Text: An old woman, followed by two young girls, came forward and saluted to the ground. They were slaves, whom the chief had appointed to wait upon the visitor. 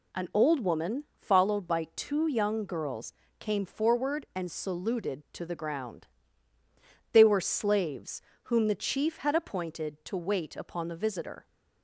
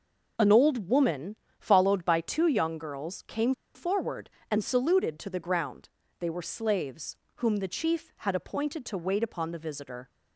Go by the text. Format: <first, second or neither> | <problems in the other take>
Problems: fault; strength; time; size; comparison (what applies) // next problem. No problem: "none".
first | pauses between "came" and "forward"; slight; at 3.5 s; 0.22 s long